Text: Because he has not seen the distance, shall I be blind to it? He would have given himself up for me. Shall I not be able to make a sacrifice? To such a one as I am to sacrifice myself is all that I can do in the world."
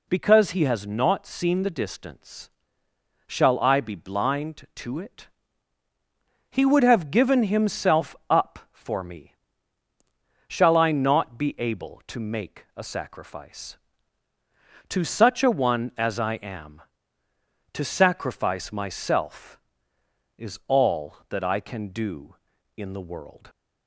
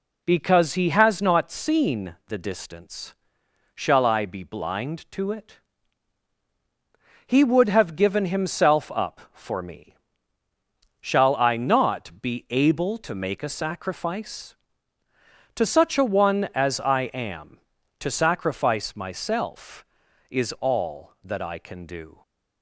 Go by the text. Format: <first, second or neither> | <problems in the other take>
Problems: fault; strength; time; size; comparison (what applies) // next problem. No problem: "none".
first | stops before "in the world"; at 22.2 s